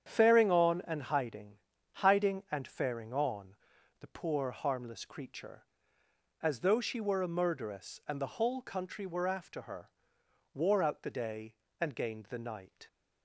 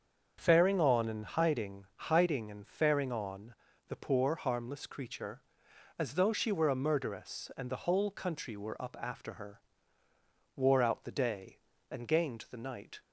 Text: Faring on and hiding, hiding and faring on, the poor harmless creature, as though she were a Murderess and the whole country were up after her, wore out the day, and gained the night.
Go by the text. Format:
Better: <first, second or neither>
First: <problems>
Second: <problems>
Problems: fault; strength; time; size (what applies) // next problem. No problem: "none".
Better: second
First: starts louder than the rest; strong; until 1.1 s; 8.5 dB // skips "up"; at 9.2 s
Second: starts louder than the rest; until 1.4 s; 7 dB